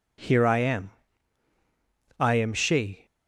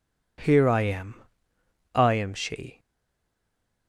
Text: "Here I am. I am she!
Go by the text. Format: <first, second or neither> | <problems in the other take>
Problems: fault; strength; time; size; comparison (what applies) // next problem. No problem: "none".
first | stays silent after the last word; from 2.7 s on; 1.1 s long